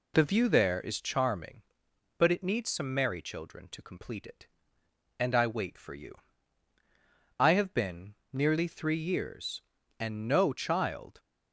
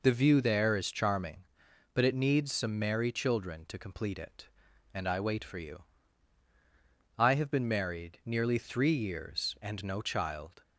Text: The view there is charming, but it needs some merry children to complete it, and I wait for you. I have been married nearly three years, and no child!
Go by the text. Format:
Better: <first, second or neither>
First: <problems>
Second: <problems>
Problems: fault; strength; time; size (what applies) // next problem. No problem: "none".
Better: second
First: skips "married"; at 8.2 s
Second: none